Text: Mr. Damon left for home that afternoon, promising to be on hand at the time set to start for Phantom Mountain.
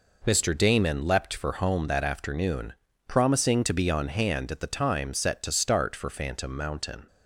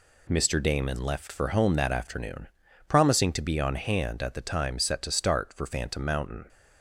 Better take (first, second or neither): second